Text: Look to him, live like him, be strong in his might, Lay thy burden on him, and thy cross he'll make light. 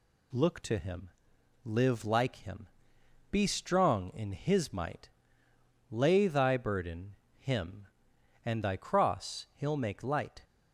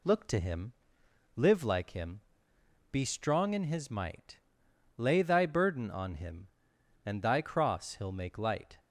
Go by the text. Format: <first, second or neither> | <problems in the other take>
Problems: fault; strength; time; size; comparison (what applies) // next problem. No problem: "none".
second | skips "on"; at 7.2 s